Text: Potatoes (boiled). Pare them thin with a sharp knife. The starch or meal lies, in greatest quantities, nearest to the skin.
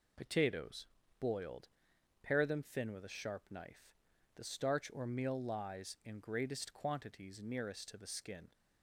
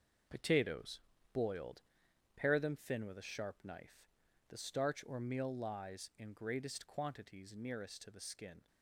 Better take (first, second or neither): first